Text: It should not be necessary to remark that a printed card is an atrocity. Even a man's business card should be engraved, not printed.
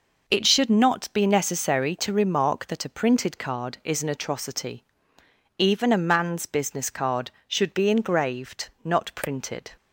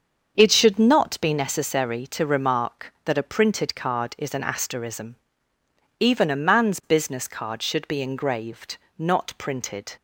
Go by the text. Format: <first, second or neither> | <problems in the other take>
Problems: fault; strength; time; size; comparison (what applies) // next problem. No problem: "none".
first | starts louder than the rest; until 1.3 s; 7 dB // says "asterism" for "atrocity"; at 4.4 s